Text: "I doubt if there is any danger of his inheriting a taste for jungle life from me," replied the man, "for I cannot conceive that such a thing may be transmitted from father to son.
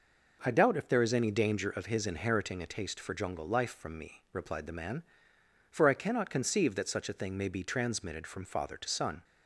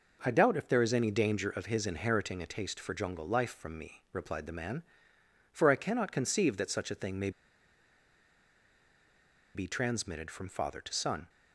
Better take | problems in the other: first | pauses between "may" and "be"; strong; at 7.3 s; 2.2 s long

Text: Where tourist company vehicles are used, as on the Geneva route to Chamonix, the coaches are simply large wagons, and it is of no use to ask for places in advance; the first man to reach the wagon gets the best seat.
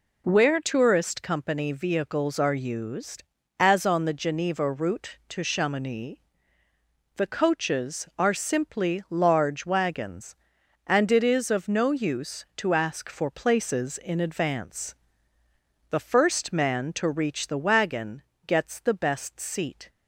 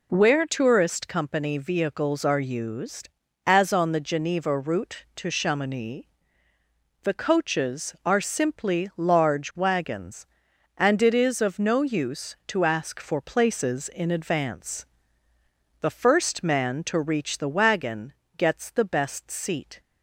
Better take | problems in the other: neither | pauses between "wagon" and "gets"; slight; the same in both

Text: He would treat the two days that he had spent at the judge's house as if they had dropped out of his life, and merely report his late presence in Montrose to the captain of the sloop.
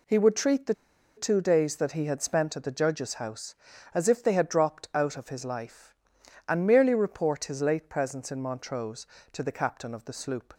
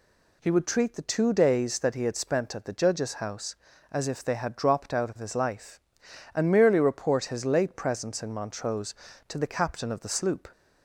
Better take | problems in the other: second | pauses between "the" and "two"; at 0.7 s; 0.42 s long

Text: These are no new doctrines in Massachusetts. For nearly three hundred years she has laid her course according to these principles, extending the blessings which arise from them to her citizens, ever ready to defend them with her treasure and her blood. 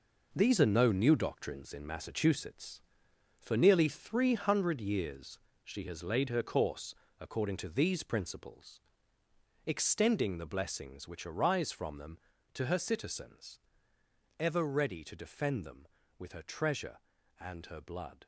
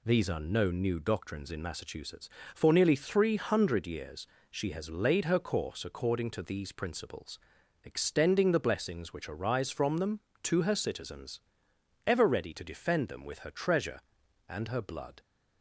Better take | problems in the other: second | gets quieter; strong; throughout; 9 dB // pauses between "years" and "she"; slight; at 5.3 s; 0.26 s long; slight in the second // pauses between "course" and "according"; slight; at 6.9 s; 0.24 s long

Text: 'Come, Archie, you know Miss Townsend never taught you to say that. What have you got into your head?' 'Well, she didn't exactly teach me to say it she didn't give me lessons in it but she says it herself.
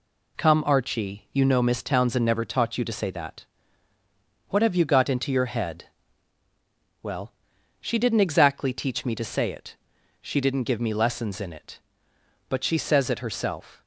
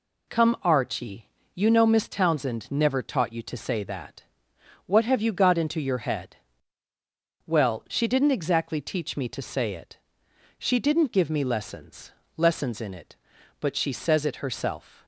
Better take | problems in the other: first | pauses between "it" and "she"; noticeable; at 9.9 s; 0.62 s long; also in the first // says "lessons" twice; at 12.3 s

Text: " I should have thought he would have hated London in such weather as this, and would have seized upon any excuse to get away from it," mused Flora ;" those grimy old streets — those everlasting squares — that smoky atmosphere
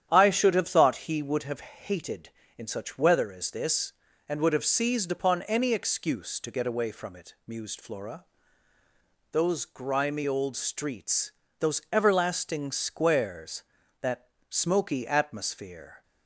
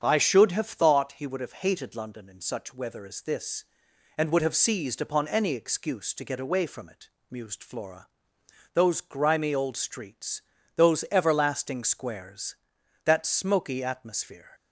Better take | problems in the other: second | starts louder than the rest; strong; until 1.1 s; 10.5 dB; strong in the second // skips "London"; at 2.4 s // pauses between "that" and "smoky"; slight; at 14.3 s; 0.18 s long

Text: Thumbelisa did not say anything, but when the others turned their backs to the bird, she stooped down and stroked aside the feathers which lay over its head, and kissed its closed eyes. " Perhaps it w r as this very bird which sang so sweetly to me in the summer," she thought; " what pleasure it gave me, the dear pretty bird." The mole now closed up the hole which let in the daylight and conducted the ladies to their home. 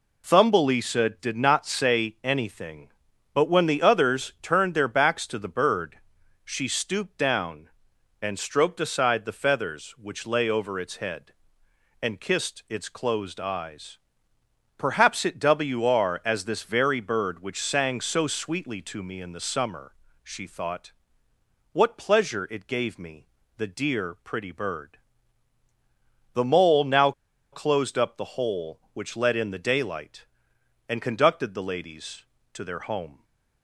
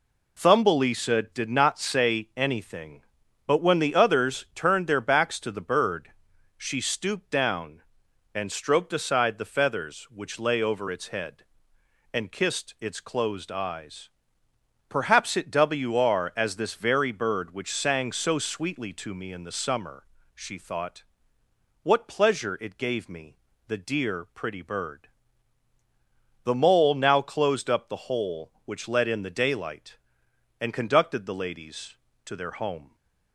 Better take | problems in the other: second | pauses between "now" and "closed"; at 27.1 s; 0.41 s long

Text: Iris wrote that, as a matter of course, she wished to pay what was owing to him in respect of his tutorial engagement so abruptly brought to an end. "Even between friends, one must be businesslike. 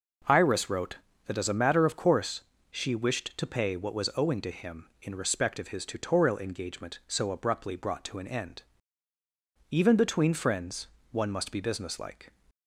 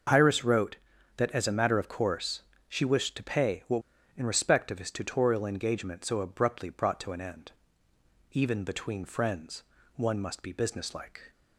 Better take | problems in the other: first | starts louder than the rest; until 1.5 s; 6 dB // skips "was owing to him"; at 3.9 s

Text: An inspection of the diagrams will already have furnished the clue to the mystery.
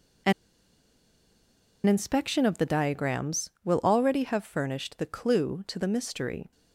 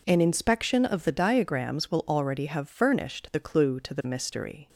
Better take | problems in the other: second | pauses between "An" and "inspection"; strong; at 0.3 s; 1.5 s long

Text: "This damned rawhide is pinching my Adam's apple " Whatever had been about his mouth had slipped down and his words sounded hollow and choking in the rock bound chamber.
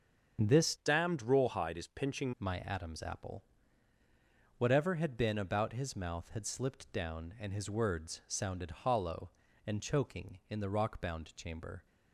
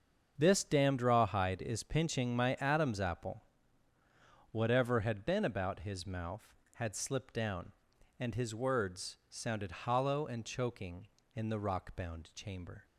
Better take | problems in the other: second | starts louder than the rest; until 1.4 s; 6.5 dB; strong in the second // changes voice from "damned" to "pinching"; from 0.7 to 2.3 s; 1.6 s long

